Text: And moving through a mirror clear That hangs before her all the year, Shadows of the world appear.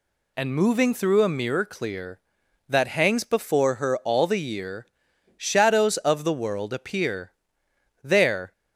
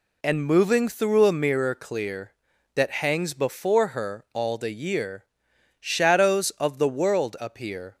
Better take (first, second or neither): second